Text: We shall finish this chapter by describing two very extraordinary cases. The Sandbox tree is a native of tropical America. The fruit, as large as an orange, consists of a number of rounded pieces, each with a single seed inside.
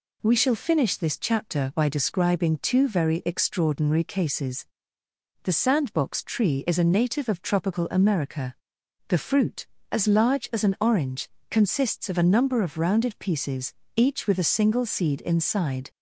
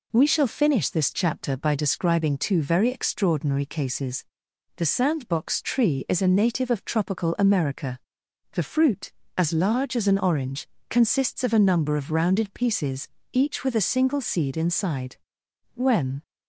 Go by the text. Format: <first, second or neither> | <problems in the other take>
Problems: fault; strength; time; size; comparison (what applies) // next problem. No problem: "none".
first | goes on to say "When"; slight; from 15.7 s on; 0.46 s long